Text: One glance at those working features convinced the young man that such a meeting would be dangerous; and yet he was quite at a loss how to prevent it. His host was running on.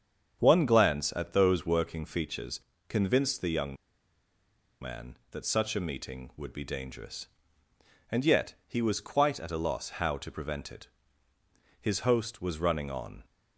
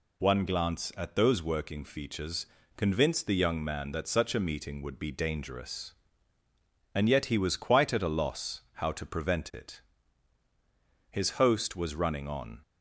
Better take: second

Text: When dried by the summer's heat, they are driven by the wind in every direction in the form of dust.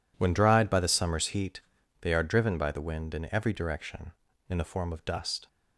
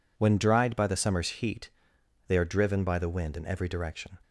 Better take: first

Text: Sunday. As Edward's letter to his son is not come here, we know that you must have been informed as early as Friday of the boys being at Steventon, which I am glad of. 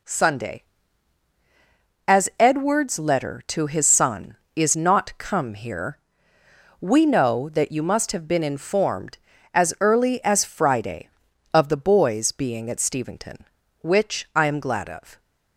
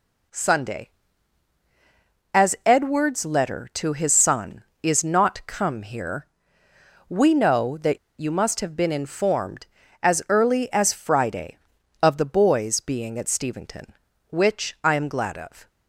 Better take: first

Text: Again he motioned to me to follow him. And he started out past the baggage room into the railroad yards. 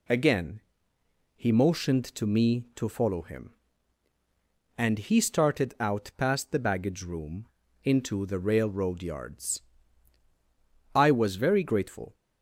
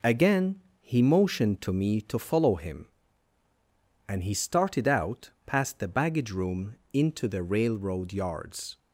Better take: second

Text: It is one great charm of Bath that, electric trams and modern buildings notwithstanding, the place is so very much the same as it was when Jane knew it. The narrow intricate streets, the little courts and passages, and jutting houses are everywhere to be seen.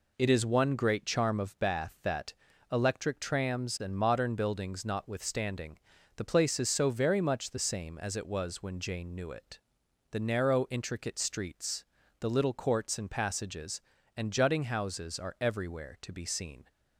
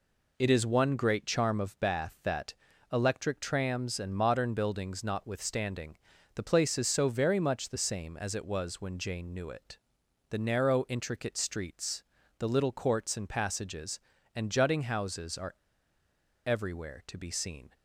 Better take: first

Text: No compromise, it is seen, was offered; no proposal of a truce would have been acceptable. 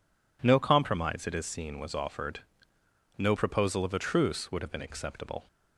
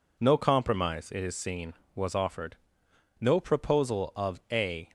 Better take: first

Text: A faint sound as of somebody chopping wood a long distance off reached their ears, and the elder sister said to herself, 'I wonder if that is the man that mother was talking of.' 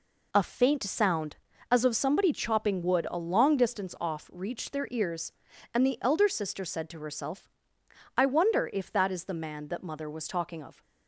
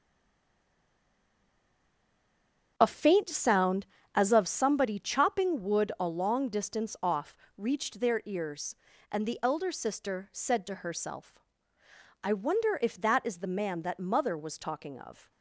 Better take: first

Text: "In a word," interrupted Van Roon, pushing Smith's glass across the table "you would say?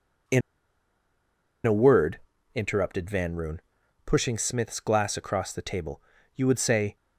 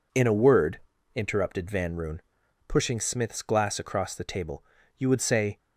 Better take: second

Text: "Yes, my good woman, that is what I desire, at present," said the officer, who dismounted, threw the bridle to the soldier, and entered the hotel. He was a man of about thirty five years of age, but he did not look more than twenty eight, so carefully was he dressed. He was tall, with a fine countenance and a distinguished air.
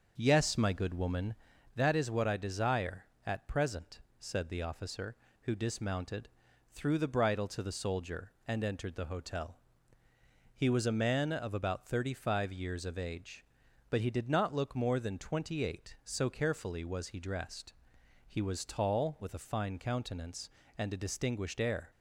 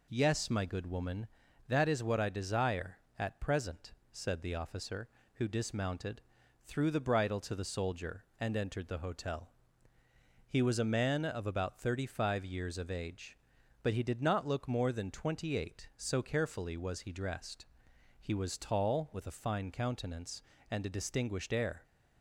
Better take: second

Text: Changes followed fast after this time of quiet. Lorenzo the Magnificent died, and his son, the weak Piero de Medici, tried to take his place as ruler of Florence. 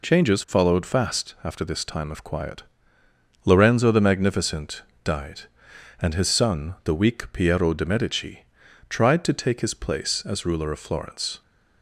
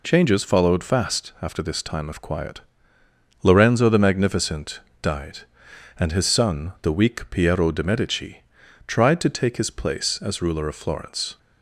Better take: neither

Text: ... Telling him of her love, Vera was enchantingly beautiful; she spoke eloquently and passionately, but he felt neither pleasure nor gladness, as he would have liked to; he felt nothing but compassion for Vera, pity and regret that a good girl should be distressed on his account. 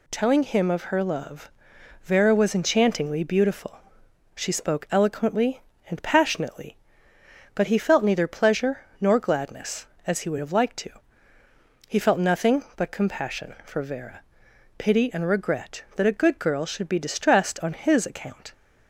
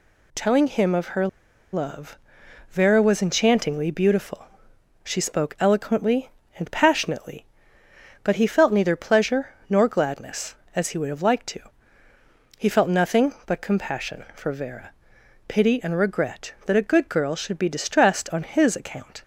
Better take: first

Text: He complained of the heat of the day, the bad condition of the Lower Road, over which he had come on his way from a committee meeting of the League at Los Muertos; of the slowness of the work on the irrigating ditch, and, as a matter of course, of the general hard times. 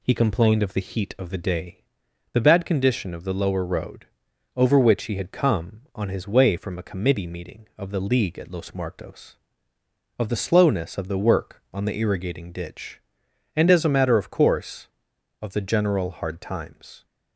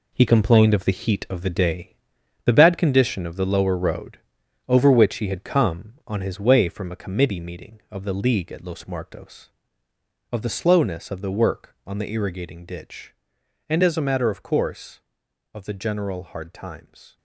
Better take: first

